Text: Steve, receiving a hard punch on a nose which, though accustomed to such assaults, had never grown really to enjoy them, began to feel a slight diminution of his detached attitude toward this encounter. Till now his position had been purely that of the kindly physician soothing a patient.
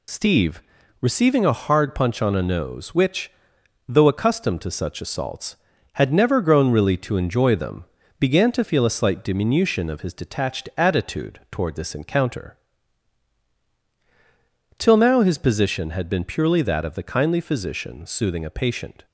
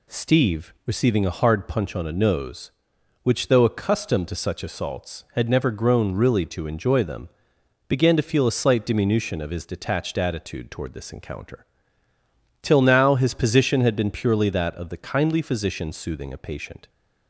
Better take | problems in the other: second | loses the start of "Steve"; at 0.0 s; 50 ms

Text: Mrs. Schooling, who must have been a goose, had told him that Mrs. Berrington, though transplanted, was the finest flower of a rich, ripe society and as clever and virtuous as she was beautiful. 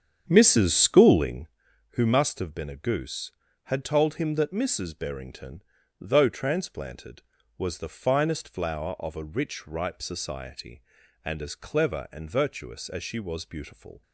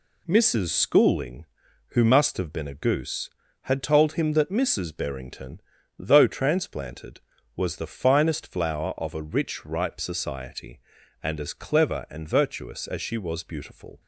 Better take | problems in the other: second | starts louder than the rest; strong; until 1.6 s; 8.5 dB

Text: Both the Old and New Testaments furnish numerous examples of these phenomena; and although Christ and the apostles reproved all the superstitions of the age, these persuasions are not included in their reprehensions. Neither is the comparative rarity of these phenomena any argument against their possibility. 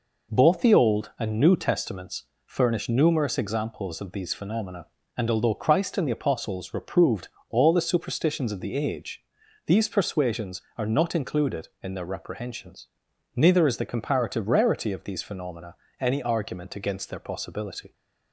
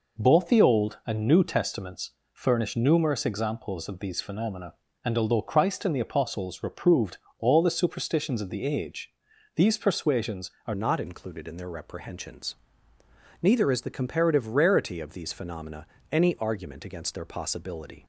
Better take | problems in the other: first | pauses between "Testaments" and "furnish"; slight; at 2.1 s; 0.20 s long; slight in the first // pauses between "reproved" and "all"; slight; at 7.1 s; 0.22 s long; slight in the first // changes voice at "not"; from 10.7 s on; 7.3 s long // pauses between "phenomena" and "any"; slight; at 15.8 s; 0.22 s long; slight in the first

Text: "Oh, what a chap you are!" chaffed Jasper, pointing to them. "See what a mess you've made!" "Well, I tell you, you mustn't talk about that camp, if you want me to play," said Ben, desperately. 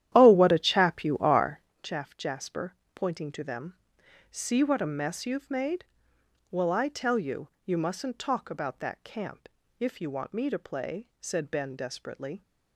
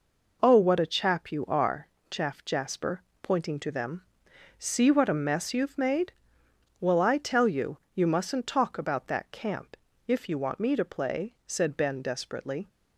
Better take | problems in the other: second | starts louder than the rest; strong; until 1.8 s; 11.5 dB

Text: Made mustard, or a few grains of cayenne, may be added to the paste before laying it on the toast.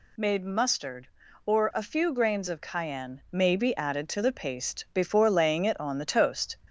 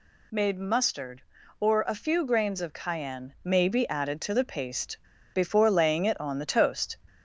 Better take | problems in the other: first | pauses between "paste" and "before"; slight; at 4.9 s; 0.36 s long

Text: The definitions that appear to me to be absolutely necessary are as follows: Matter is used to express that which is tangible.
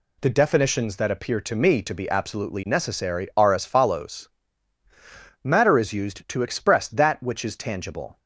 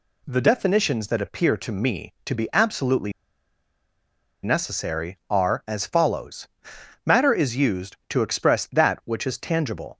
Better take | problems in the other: first | pauses between "absolutely" and "necessary"; strong; at 3.1 s; 1.3 s long

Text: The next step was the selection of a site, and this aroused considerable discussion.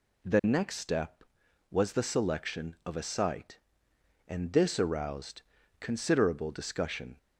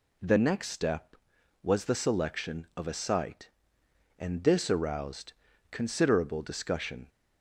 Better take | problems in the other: neither | pauses between "aroused" and "considerable"; the same in both

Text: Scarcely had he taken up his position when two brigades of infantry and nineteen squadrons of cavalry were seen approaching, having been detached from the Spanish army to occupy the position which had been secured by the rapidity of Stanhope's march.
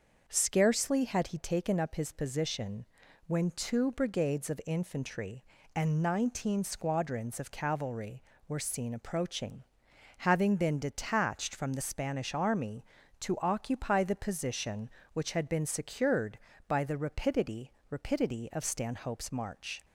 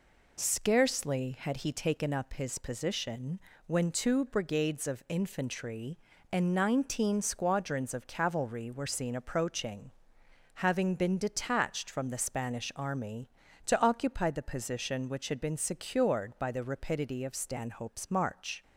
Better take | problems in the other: second | starts louder than the rest; until 1.2 s; 6.5 dB // pauses between "position" and "when"; at 2.8 s; 0.42 s long; slight in the second // says "rapidity" twice; at 17.9 s

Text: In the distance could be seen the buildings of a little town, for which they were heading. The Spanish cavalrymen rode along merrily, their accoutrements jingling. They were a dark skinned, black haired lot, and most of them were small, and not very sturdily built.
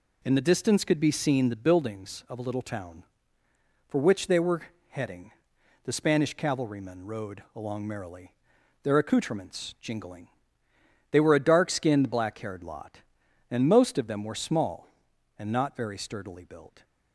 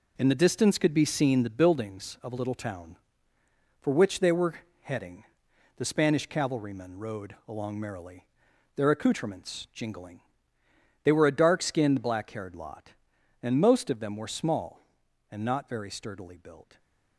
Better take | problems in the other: first | gets quieter; strong; throughout; 7.5 dB // pauses between "were" and "heading"; slight; at 4.5 s; 0.28 s long; slight in the first

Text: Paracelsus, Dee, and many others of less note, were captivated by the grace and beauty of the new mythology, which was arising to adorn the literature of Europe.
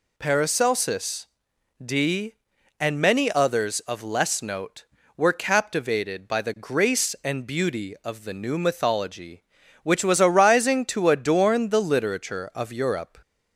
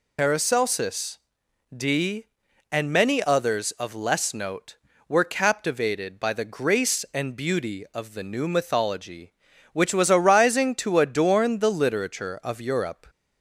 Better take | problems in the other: first | loses the start of "Paracelsus"; at 0.1 s; 90 ms

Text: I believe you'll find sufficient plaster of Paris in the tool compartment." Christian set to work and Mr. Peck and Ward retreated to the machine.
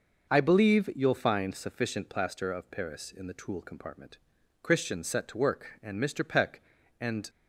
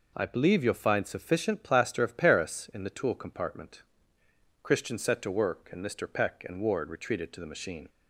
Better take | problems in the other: second | stops before "Ward retreated to the machine"; at 7.2 s

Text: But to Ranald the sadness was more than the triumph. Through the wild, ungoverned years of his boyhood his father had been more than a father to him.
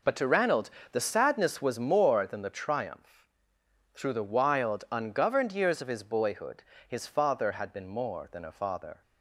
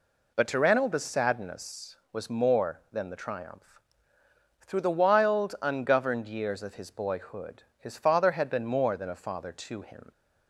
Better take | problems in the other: second | pauses between "Ranald" and "the"; slight; at 0.7 s; 0.20 s long // pauses between "boyhood" and "his"; slight; at 6.6 s; 0.24 s long; slight in the second // stops before "to him"; at 9.0 s

